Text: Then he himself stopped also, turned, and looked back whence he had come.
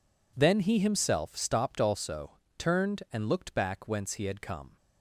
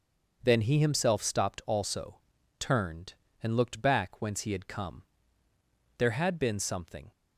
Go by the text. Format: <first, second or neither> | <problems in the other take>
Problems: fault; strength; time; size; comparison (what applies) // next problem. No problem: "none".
first | goes on to say "There had been something"; noticeable; from 5.9 s on; 1.1 s long